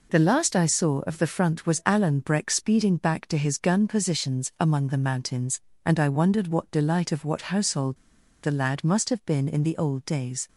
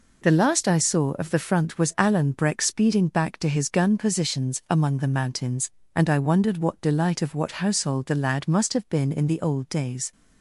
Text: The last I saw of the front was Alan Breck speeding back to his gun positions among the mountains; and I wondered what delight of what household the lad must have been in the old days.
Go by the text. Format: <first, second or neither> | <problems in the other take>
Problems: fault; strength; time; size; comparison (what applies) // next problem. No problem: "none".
second | pauses between "household" and "the"; noticeable; at 7.9 s; 0.47 s long